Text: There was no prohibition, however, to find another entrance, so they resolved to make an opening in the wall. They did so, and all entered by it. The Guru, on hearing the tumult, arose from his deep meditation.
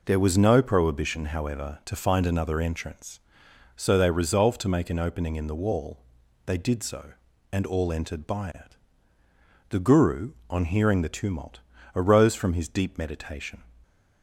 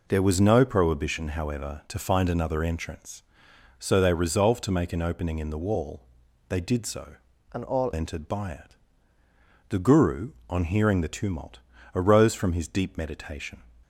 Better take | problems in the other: first | changes voice from "and" to "all"; from 7.5 to 7.8 s; 0.3 s long

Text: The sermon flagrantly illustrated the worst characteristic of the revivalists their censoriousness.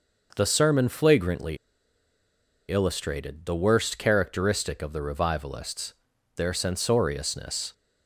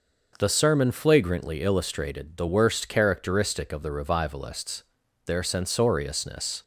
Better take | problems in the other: second | pauses between "flagrantly" and "illustrated"; at 1.5 s; 1.1 s long // pauses between "revivalists" and "their"; at 5.9 s; 0.44 s long; also in the second

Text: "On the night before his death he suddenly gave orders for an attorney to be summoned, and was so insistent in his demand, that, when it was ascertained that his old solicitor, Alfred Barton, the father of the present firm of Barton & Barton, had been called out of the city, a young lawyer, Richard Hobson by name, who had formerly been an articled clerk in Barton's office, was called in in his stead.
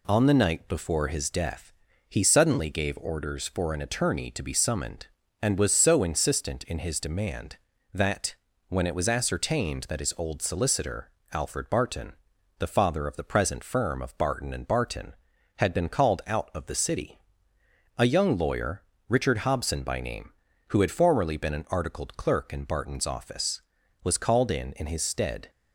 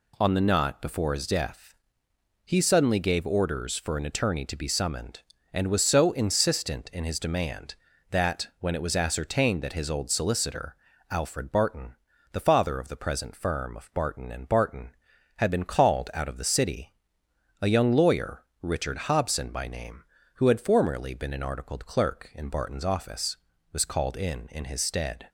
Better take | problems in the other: first | says "knot" for "night"; at 0.4 s // pauses between "death" and "he"; noticeable; at 1.7 s; 0.70 s long; slight in the first

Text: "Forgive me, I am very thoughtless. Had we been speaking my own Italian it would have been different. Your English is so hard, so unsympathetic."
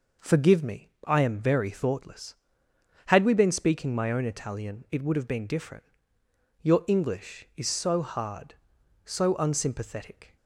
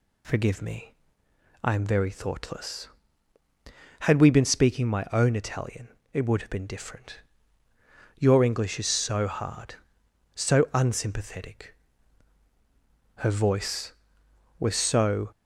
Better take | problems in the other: first | pauses between "Italian" and "it"; slight; at 5.8 s; 0.26 s long // goes on to say "Her voice was so"; strong; from 13.1 s on; 2.1 s long

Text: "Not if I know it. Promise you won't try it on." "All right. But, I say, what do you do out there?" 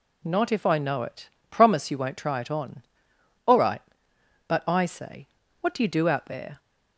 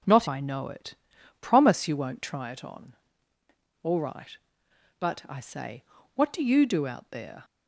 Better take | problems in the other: first | skips "if"; at 0.2 s

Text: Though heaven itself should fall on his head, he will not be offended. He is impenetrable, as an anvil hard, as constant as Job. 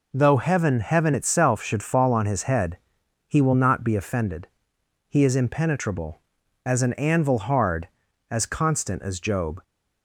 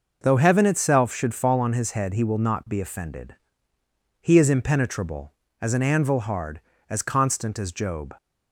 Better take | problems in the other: second | says "heaven" twice; at 0.8 s

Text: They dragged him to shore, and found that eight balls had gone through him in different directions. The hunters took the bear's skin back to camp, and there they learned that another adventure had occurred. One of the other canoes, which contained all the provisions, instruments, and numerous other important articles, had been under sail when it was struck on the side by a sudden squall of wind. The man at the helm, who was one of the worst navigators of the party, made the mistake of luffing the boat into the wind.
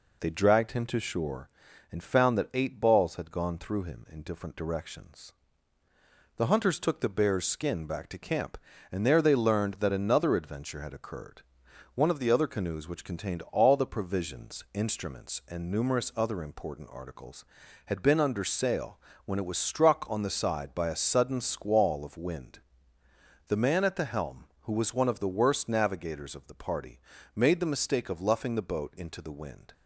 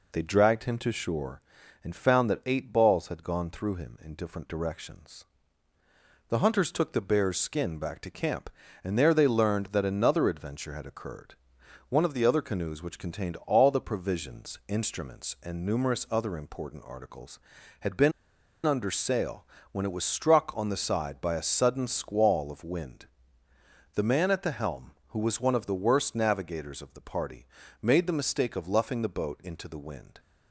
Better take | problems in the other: first | pauses between "been" and "under"; noticeable; at 18.1 s; 0.53 s long // pauses between "sail" and "when"; slight; at 19.4 s; 0.26 s long; slight in the first

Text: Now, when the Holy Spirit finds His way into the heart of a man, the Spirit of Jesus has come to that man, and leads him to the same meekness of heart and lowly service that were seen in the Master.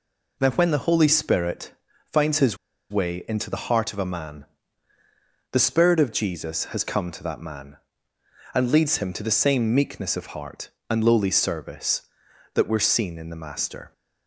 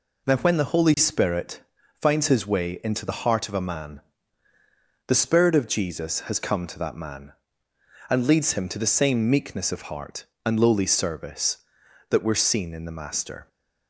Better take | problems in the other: second | pauses between "Spirit" and "finds"; slight; at 1.7 s; 0.34 s long; slight in the second // pauses between "His" and "way"; slight; at 2.5 s; 0.33 s long

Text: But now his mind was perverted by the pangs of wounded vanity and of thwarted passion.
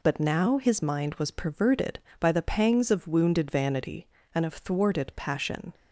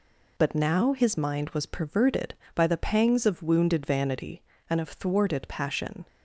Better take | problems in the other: neither | none

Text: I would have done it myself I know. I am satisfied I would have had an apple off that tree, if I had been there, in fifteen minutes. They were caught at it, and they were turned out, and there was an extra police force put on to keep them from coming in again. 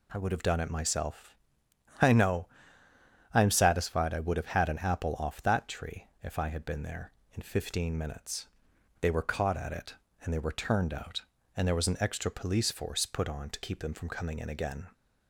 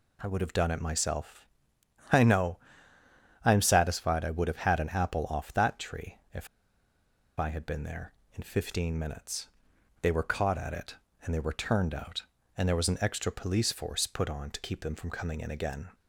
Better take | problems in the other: first | pauses between "myself" and "I"; noticeable; at 1.4 s; 0.66 s long; noticeable in the first // pauses between "if" and "I"; noticeable; at 6.4 s; 0.92 s long

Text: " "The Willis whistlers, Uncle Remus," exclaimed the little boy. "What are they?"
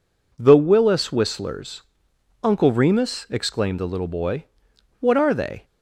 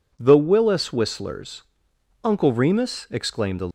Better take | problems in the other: first | stops before "little boy What are they"; at 3.6 s

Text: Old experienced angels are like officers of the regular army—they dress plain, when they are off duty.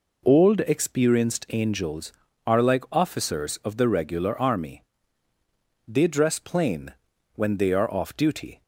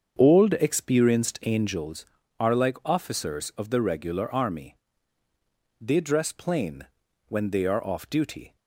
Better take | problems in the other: first | starts louder than the rest; until 1.8 s; 7 dB

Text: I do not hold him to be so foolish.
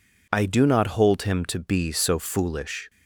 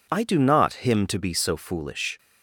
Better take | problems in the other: first | skips "hold"; at 0.8 s

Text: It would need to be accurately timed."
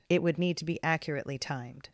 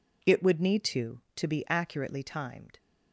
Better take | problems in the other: first | says "to" twice; at 1.3 s

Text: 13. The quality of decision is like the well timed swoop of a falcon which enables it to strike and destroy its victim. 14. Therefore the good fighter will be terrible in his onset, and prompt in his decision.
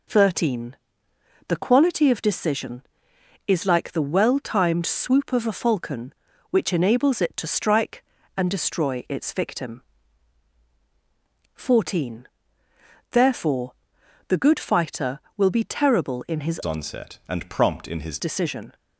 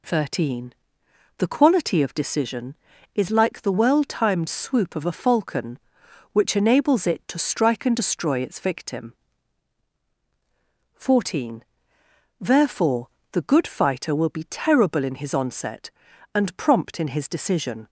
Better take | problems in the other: second | pauses between "Therefore" and "the"; noticeable; at 13.7 s; 0.56 s long; slight in the second // changes voice from "onset" to "his"; from 16.6 to 18.1 s; 1.5 s long

